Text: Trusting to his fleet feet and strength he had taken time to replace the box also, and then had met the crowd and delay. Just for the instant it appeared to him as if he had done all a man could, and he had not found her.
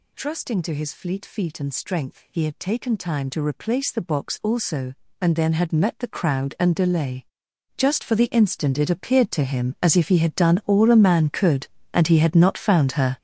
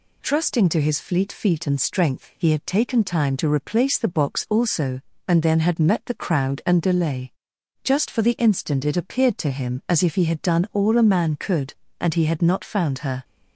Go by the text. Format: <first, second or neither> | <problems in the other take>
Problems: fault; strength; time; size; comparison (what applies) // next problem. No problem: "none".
second | gets louder; strong; throughout; 11 dB